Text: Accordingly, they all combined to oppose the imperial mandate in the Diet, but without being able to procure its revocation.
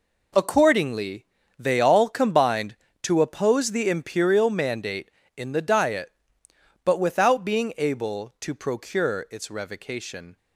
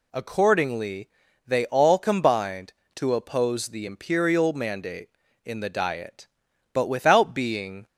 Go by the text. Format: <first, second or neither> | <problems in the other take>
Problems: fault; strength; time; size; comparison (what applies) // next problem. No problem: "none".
first | stops before "able to procure its revocation"; at 7.8 s